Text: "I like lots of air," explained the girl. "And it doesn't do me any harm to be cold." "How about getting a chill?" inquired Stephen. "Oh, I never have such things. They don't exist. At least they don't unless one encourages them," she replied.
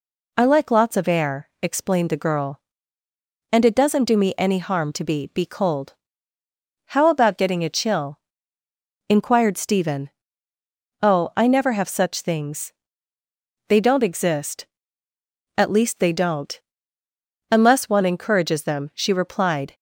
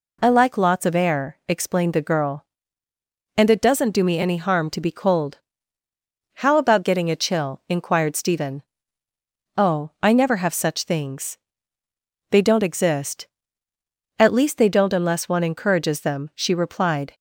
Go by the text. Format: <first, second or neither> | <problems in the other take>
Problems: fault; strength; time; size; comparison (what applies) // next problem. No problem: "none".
second | says "be" twice; at 5.2 s // pauses between "don't" and "unless"; noticeable; at 16.5 s; 0.92 s long